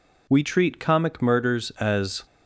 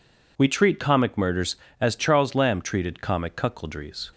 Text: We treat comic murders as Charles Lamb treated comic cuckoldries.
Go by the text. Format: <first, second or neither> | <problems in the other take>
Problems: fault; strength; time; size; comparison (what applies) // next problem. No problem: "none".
second | stops before "Charles Lamb treated comic cuckoldries"; at 2.2 s